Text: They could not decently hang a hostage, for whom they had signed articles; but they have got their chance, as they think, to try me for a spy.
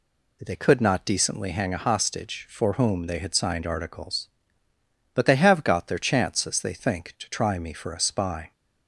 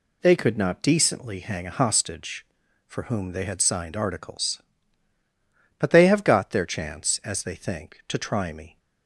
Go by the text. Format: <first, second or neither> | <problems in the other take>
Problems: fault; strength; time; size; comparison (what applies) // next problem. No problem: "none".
first | stops before "for a spy"; at 8.7 s